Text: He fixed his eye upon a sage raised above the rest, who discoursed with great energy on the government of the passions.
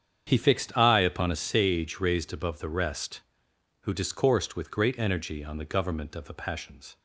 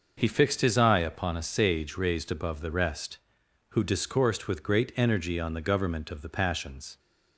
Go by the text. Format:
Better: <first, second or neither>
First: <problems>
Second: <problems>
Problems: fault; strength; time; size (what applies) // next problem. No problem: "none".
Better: second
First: starts louder than the rest; strong; until 1.2 s; 8 dB // skips "his"; at 0.7 s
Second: none